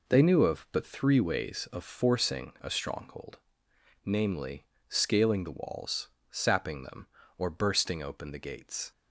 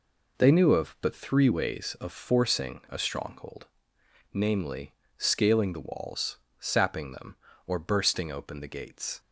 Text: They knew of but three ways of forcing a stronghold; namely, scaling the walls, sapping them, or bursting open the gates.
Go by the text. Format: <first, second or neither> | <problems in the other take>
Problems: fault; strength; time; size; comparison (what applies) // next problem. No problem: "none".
neither | none